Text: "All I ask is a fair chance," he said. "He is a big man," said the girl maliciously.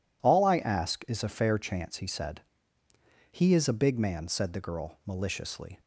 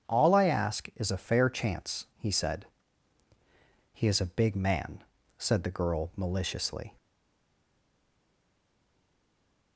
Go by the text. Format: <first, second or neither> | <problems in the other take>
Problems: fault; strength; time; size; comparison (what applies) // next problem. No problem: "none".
first | starts louder than the rest; strong; until 1.1 s; 8 dB // stays silent after the last word; strong; from 6.9 s on; 2.8 s long